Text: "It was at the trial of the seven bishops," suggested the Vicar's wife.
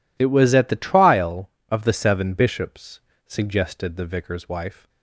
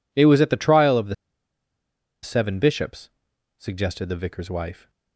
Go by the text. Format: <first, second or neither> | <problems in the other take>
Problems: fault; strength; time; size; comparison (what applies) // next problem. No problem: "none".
first | pauses between "the" and "seven"; at 1.1 s; 1.0 s long